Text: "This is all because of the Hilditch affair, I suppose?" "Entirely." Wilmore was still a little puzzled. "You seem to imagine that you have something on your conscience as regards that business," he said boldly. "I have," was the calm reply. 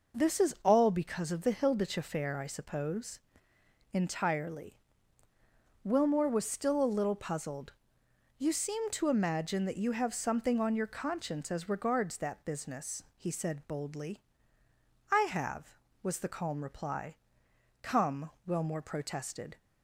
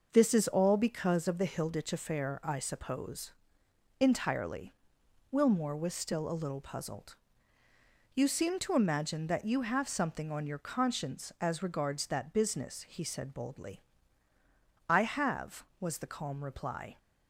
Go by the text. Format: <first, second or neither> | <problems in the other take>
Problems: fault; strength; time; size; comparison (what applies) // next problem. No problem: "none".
second | goes on to say "Come Wilmore protested"; strong; from 17.8 s on; 1.7 s long